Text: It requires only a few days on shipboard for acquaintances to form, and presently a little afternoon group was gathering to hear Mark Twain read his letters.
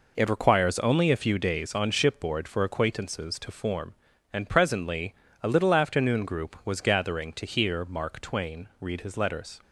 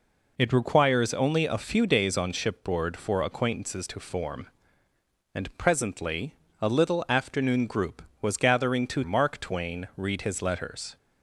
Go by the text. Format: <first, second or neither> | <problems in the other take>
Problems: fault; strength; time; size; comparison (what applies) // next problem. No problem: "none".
first | pauses between "presently" and "a"; slight; at 6.3 s; 0.26 s long; slight in the first // skips "hear"; at 9.0 s